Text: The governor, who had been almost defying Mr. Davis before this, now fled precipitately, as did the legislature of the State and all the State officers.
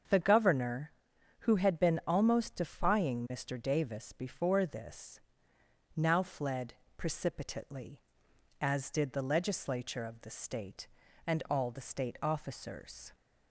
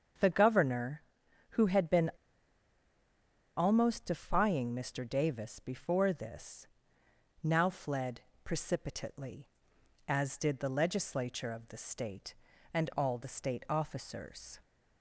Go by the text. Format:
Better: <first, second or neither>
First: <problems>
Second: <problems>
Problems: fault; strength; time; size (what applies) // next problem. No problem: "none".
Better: first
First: starts louder than the rest; until 1.5 s; 7 dB // pauses between "fled" and "precipitately"; slight; at 6.7 s; 0.24 s long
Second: starts louder than the rest; until 1.6 s; 7 dB // pauses between "been" and "almost"; strong; at 2.1 s; 1.4 s long // pauses between "fled" and "precipitately"; slight; at 8.1 s; 0.24 s long